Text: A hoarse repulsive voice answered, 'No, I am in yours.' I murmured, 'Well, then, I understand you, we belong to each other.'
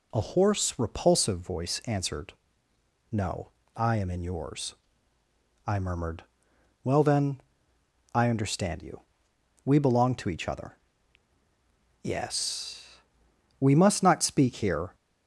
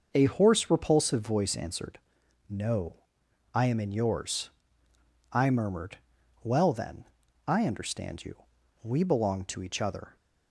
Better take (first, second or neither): second